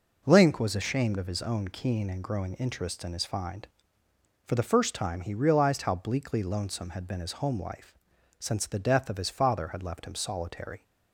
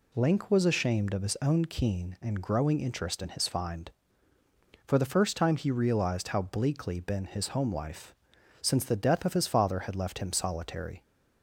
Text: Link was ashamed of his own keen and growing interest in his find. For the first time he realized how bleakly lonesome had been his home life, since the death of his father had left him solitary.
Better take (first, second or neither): first